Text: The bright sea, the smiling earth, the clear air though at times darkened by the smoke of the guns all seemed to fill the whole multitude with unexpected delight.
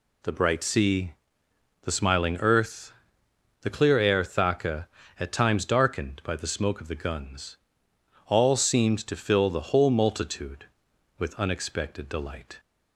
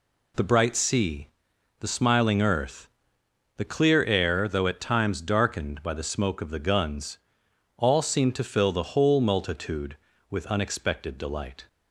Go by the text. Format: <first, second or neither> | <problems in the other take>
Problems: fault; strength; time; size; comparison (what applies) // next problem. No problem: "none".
second | says "thaka" for "though"; at 4.2 s // pauses between "guns" and "all"; noticeable; at 7.5 s; 0.70 s long; noticeable in the second